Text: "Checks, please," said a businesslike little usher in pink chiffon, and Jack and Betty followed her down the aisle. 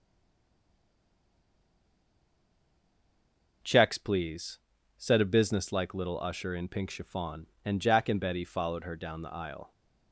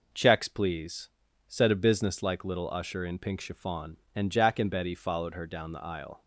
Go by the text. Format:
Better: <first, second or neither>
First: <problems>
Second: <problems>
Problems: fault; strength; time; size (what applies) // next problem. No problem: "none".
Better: second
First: stays silent before the first word; strong; until 3.6 s; 3.6 s long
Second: none